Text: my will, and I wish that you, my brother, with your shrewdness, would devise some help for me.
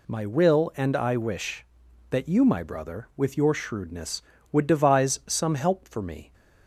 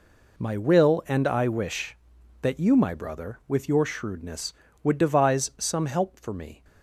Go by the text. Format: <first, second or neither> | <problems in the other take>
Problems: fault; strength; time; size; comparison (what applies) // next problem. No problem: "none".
first | gets quieter; strong; throughout; 11 dB